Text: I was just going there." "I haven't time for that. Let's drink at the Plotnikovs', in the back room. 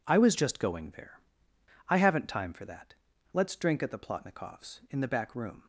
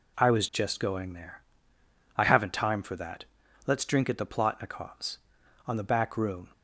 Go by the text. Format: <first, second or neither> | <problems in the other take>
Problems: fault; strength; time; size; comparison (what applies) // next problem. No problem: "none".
first | says "on" for "in"; at 5.6 s